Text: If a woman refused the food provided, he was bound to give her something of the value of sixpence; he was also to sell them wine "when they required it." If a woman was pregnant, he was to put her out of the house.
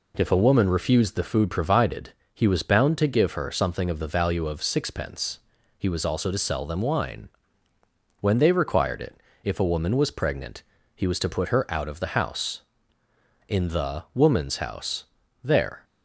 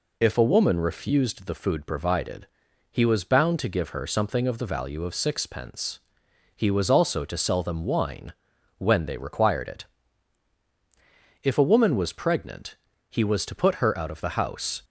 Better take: second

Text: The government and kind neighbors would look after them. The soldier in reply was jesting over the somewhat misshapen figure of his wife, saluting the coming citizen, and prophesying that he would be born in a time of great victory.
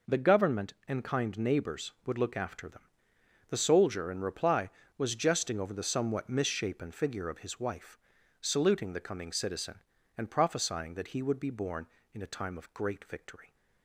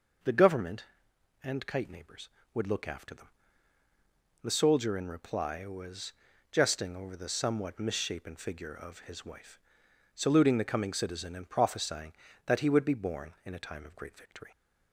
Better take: first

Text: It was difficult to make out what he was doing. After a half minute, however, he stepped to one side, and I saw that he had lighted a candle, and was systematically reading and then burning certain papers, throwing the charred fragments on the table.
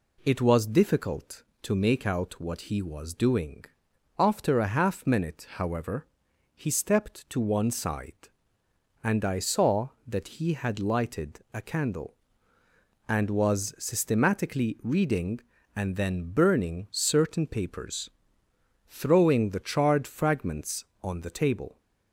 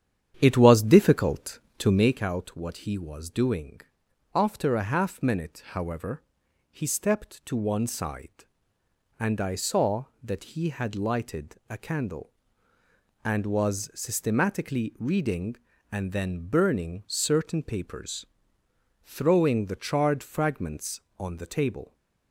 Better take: first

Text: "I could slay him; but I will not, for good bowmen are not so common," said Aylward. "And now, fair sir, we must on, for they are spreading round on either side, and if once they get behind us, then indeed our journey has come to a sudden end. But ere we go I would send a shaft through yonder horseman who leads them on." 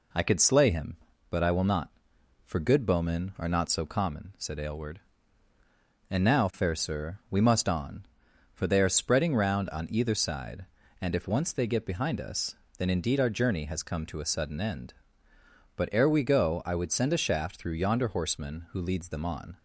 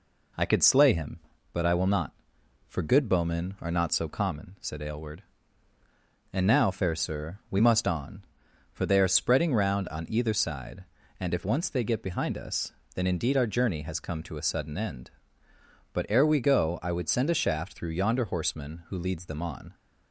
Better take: neither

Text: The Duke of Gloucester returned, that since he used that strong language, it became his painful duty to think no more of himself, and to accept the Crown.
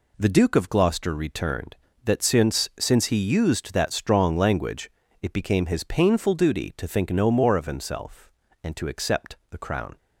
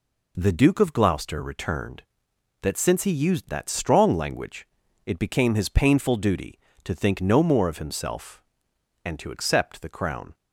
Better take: second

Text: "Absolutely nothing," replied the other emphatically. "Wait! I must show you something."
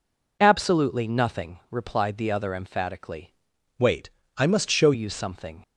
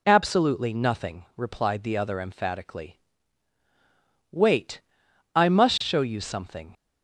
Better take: second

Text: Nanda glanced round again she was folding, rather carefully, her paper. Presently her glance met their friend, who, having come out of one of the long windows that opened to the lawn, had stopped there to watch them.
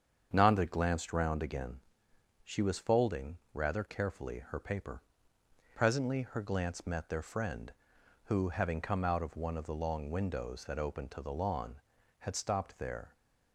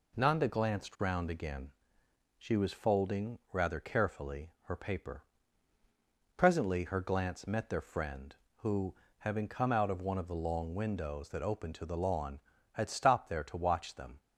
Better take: second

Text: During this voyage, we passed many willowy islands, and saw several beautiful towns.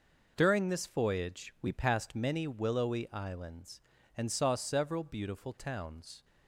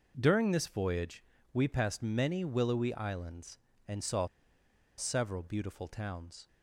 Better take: first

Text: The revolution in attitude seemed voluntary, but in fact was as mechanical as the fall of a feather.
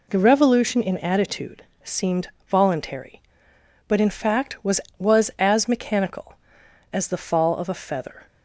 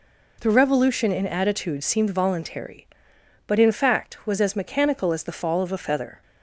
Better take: second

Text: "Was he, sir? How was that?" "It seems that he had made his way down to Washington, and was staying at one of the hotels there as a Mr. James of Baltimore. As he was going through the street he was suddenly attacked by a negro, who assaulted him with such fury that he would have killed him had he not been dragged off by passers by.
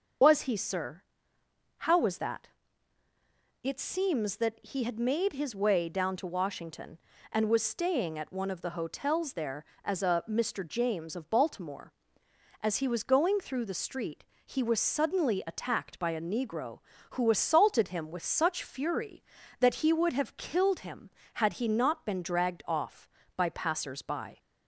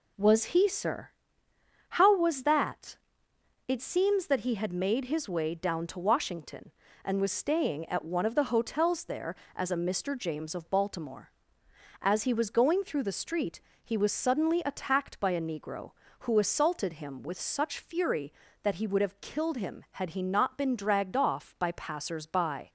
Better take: second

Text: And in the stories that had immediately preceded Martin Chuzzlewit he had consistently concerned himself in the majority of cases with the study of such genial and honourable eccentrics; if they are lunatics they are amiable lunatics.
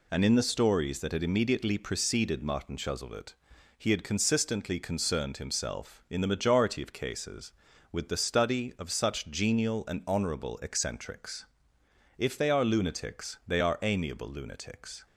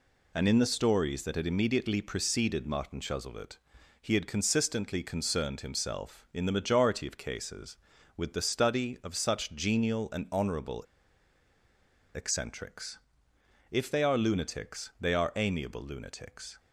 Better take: first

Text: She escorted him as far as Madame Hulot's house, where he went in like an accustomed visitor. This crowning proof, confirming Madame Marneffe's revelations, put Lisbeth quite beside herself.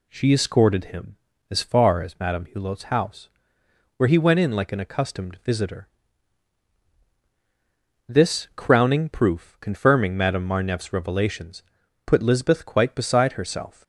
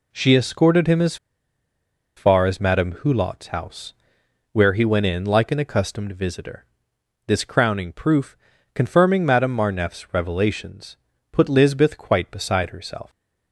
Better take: first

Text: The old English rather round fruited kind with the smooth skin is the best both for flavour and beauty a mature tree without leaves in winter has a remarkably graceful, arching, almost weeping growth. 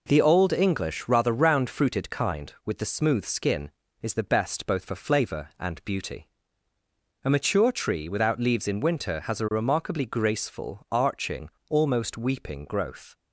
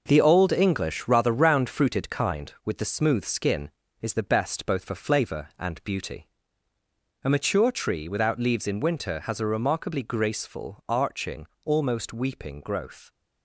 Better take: first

